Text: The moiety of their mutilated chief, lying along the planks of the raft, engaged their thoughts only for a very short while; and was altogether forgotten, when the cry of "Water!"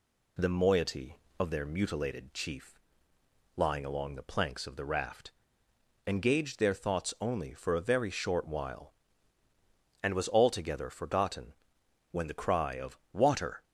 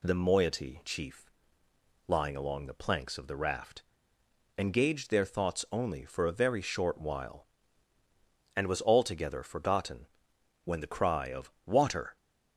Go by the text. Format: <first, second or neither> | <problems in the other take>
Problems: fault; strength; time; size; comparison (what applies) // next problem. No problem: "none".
first | skips "of their mutilated"; at 0.8 s // pauses between "of" and "Water"; slight; at 11.5 s; 0.16 s long; slight in the first